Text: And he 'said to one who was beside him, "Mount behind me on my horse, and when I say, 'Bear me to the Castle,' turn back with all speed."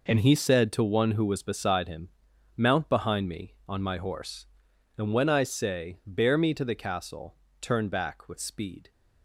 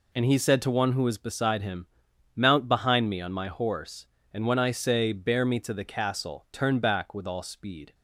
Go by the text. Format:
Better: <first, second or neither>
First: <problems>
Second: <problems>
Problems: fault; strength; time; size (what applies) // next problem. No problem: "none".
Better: second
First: skips "all"; at 8.3 s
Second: none